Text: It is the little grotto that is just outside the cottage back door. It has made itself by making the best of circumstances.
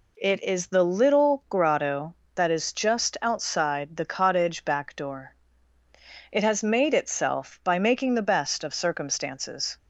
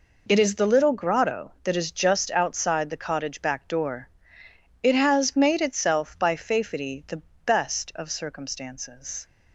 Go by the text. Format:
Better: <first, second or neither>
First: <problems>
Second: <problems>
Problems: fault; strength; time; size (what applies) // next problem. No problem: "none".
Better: first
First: none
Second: says "fafety" for "making"; at 6.3 s // pauses between "the" and "best"; slight; at 7.2 s; 0.24 s long